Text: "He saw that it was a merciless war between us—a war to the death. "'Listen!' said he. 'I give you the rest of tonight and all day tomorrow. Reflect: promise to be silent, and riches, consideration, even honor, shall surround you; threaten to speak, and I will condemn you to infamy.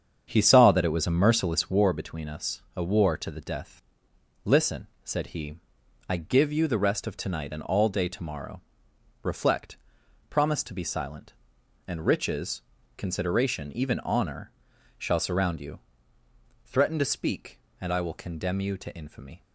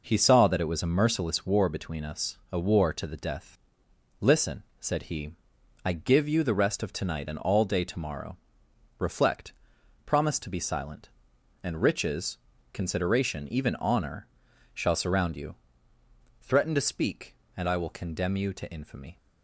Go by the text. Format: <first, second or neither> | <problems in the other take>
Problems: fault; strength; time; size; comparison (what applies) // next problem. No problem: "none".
second | starts louder than the rest; strong; until 2.0 s; 7.5 dB